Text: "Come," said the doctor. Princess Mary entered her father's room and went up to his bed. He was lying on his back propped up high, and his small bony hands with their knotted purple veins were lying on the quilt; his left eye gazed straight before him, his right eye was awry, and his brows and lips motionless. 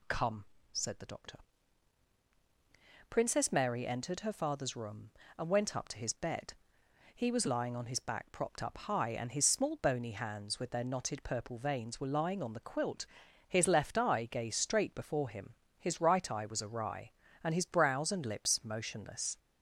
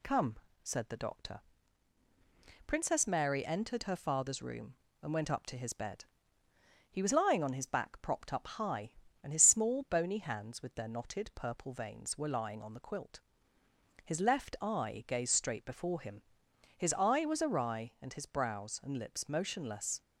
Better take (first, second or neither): first